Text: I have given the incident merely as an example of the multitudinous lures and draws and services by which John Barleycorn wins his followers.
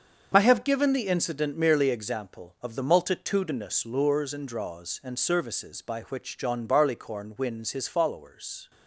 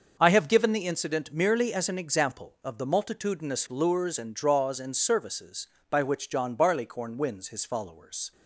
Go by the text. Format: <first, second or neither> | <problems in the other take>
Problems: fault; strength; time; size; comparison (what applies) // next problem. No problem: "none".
second | starts louder than the rest; until 1.3 s; 6.5 dB; also in the second // skips "as an"; at 1.9 s